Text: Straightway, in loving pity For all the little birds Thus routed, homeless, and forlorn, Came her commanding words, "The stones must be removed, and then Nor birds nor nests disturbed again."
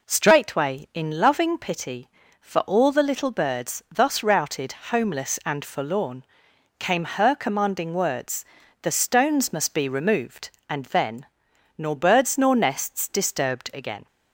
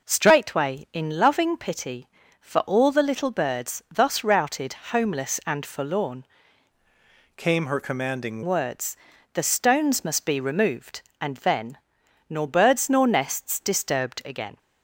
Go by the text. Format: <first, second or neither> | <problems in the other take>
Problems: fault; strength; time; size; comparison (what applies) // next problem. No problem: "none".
first | changes voice from "Came" to "commanding"; from 7.3 to 8.4 s; 1.1 s long // pauses between "then" and "Nor"; noticeable; at 11.7 s; 0.50 s long; noticeable in the first